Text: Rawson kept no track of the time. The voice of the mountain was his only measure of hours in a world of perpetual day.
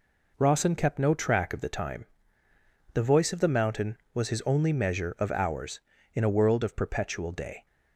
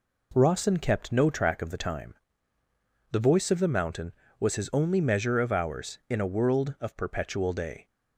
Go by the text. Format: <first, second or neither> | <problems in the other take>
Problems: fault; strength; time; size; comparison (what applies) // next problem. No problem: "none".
neither | none